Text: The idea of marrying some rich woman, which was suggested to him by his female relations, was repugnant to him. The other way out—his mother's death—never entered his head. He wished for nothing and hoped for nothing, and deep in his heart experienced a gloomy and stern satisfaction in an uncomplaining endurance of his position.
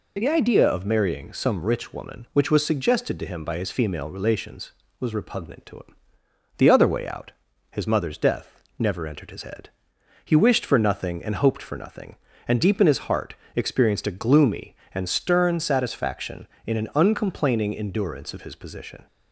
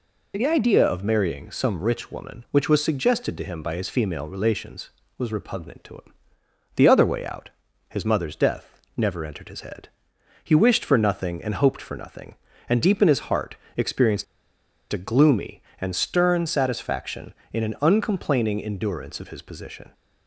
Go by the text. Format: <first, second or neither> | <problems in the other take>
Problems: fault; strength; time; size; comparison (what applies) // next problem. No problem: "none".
first | pauses between "heart" and "experienced"; slight; at 13.5 s; 0.22 s long; slight in the first // pauses between "experienced" and "a"; noticeable; at 14.2 s; 0.68 s long